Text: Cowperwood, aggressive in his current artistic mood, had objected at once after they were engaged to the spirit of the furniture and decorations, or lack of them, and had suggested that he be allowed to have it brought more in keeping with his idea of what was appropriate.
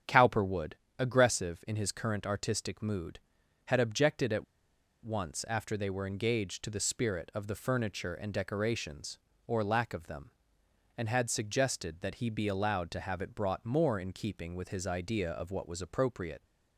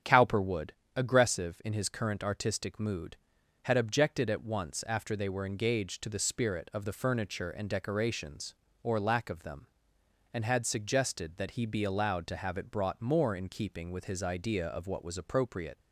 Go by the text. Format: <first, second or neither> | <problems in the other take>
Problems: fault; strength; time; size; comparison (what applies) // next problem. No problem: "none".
second | starts louder than the rest; strong; until 1.3 s; 8.5 dB; strong in the second // pauses between "at" and "once"; noticeable; at 4.4 s; 0.58 s long